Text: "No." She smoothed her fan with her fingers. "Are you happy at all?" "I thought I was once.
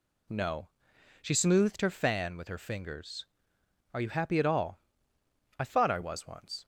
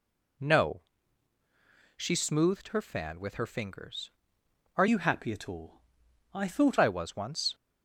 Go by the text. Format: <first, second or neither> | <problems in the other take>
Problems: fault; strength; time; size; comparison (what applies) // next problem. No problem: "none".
first | changes voice from "you" to "thought"; from 4.8 to 6.7 s; 1.9 s long